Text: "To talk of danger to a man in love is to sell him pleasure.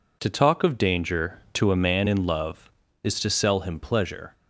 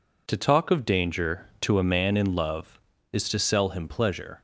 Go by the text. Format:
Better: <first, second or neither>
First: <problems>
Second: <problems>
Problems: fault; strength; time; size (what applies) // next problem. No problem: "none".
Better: neither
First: none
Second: none